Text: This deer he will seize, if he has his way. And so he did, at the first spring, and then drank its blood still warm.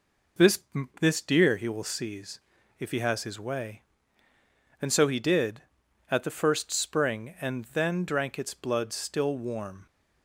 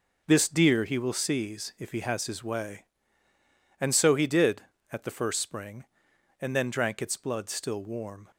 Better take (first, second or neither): second